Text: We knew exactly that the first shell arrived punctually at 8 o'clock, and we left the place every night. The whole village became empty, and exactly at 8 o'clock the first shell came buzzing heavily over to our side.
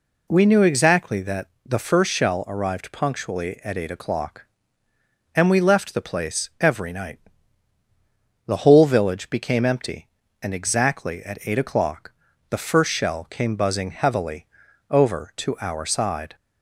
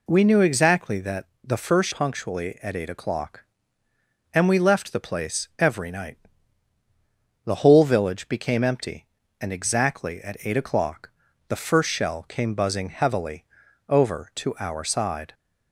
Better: first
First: pauses between "that" and "the"; slight; at 1.4 s; 0.16 s long // pauses between "o'clock" and "the"; at 12.1 s; 0.38 s long // pauses between "heavily" and "over"; at 14.4 s; 0.44 s long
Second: pauses between "that" and "the"; slight; at 1.2 s; 0.16 s long // skips "shell arrived"; at 1.9 s // pauses between "o'clock" and "the"; at 11.0 s; 0.38 s long // pauses between "heavily" and "over"; at 13.4 s; 0.44 s long

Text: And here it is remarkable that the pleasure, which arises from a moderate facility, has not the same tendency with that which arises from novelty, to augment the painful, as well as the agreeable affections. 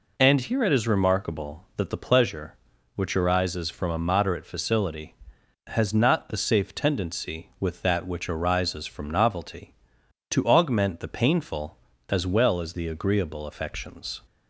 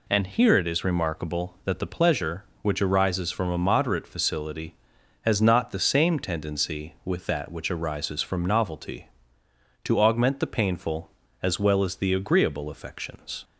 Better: second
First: says "safe" for "same"; at 6.3 s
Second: none

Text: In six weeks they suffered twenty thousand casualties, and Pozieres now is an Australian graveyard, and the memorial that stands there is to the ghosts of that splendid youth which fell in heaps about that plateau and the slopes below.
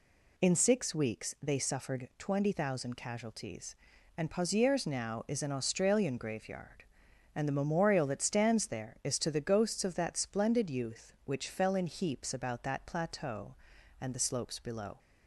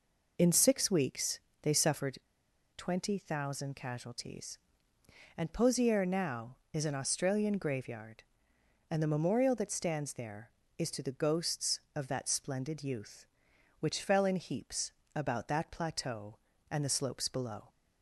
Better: first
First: none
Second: pauses between "weeks" and "they"; slight; at 1.4 s; 0.20 s long // pauses between "suffered" and "twenty"; noticeable; at 2.1 s; 0.58 s long // pauses between "heaps" and "about"; slight; at 14.9 s; 0.24 s long

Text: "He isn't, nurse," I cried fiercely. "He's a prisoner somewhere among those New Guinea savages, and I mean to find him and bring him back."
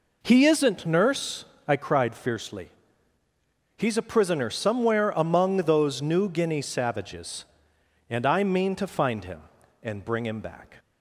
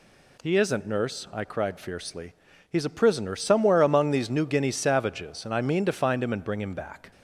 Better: first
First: none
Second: says "these" for "those"; at 4.1 s

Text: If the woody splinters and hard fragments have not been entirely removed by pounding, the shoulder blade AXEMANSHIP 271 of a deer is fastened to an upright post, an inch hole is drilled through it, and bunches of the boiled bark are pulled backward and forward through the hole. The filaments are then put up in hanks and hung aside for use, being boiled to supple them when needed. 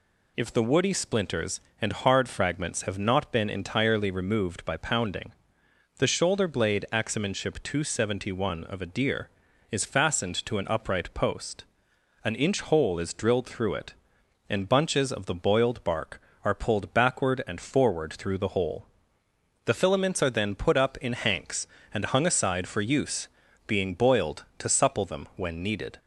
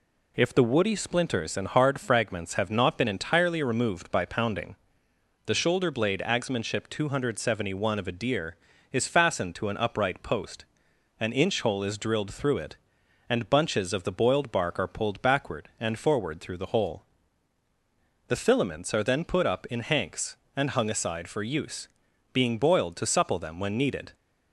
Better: neither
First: none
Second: none

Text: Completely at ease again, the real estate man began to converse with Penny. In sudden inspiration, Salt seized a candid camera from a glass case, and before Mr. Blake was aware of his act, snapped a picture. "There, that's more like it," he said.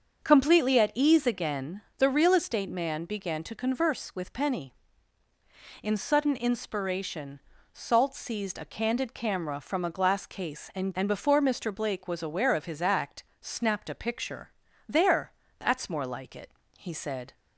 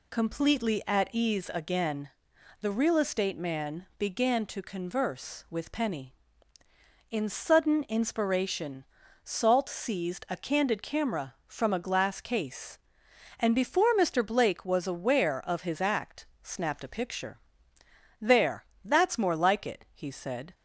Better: second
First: starts louder than the rest; until 1.2 s; 6.5 dB // says "and" twice; at 10.9 s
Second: none

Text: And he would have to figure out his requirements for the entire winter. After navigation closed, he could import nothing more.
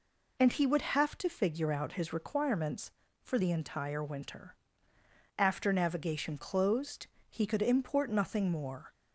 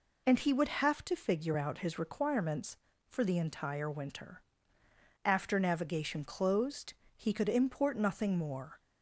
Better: neither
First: none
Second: none

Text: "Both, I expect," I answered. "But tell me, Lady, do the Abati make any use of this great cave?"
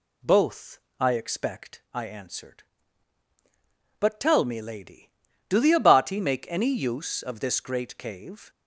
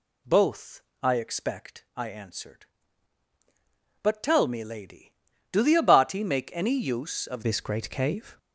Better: first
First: none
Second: changes voice at "this"; from 7.4 s on; 0.9 s long

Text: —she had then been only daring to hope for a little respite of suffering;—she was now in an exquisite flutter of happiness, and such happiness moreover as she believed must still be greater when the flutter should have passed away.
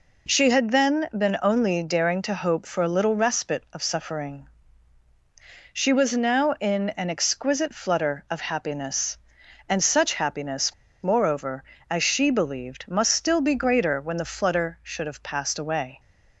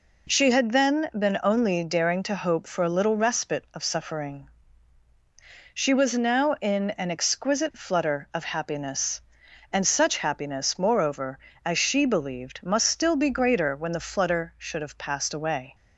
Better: second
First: pauses between "happiness" and "moreover"; slight; at 10.7 s; 0.29 s long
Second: none

